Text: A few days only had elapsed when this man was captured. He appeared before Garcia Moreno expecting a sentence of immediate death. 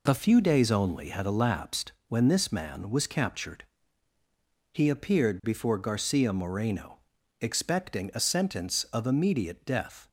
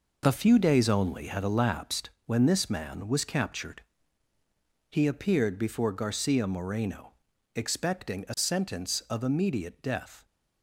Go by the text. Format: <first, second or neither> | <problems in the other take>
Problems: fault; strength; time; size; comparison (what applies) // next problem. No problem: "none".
first | gets quieter; strong; throughout; 8 dB // pauses between "elapsed" and "when"; slight; at 2.0 s; 0.16 s long; slight in the first // pauses between "Moreno" and "expecting"; at 7.1 s; 0.42 s long; also in the first